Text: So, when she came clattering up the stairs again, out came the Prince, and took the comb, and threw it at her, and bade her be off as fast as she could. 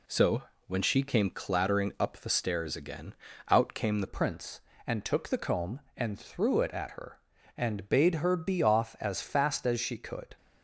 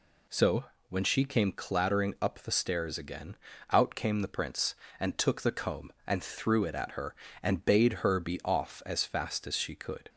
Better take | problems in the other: second | changes voice at "Prince"; from 4.0 s on; 6.3 s long

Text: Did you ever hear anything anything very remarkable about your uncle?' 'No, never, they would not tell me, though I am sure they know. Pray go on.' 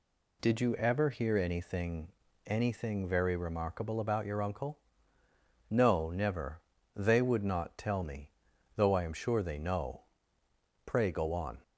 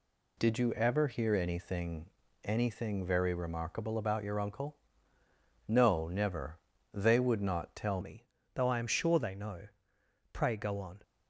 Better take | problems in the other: first | pauses between "anything" and "anything"; at 2.0 s; 0.38 s long; also in the first // changes voice at "me"; from 8.0 s on; 3.0 s long

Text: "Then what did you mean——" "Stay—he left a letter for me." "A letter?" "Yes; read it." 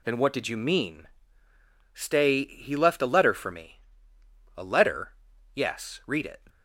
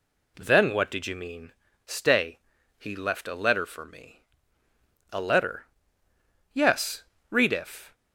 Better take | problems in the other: first | says "if" for "it"; at 7.5 s

